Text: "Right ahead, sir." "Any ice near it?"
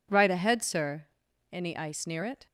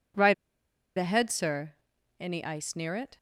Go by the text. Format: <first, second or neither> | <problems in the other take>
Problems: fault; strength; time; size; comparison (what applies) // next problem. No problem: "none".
first | pauses between "Right" and "ahead"; noticeable; at 0.3 s; 0.64 s long